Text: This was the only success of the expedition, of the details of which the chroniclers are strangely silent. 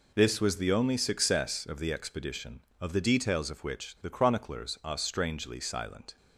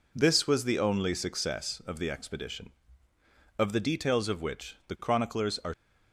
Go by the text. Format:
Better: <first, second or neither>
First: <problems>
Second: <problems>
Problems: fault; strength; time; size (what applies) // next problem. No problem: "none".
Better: first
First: none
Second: stops before "strangely silent"; at 5.7 s